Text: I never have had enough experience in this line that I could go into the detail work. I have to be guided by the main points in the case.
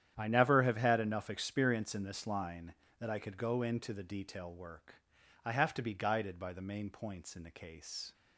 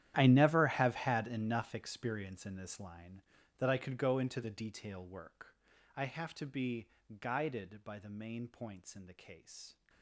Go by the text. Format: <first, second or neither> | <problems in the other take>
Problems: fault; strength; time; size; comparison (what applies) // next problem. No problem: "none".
first | gets quieter; strong; throughout; 18.5 dB // starts louder than the rest; strong; until 1.1 s; 11.5 dB; strong in the first // pauses between "be" and "guided"; slight; at 6.8 s; 0.32 s long